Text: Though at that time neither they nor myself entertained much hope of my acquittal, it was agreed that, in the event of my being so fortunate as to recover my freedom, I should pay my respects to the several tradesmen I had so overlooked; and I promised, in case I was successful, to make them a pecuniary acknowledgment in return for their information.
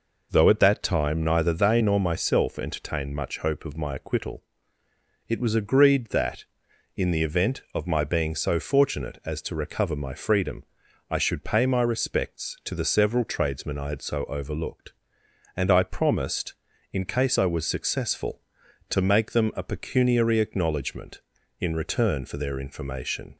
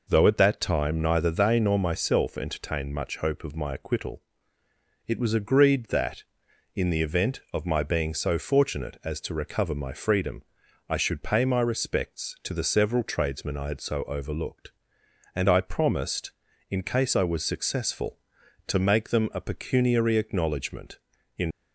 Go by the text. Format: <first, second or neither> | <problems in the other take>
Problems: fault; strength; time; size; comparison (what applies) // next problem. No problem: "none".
first | stops before "return for their information"; at 21.5 s